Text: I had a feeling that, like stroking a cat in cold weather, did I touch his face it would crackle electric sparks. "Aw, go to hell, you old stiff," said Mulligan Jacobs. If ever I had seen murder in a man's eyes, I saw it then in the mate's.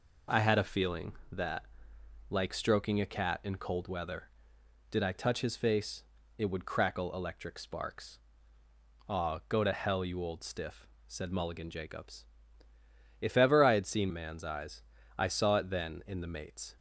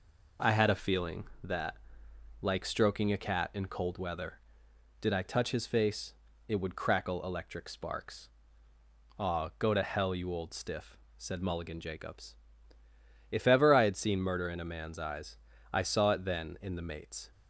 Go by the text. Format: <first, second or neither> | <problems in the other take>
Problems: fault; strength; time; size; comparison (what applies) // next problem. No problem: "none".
second | pauses between "face" and "it"; slight; at 6.0 s; 0.34 s long; slight in the second // skips "murder in a"; at 14.1 s